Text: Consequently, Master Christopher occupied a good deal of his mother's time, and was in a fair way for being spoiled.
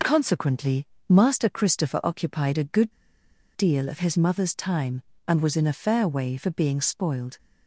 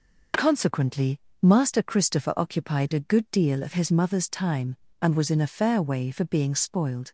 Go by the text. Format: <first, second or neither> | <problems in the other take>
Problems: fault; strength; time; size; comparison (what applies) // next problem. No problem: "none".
second | pauses between "good" and "deal"; noticeable; at 2.9 s; 0.65 s long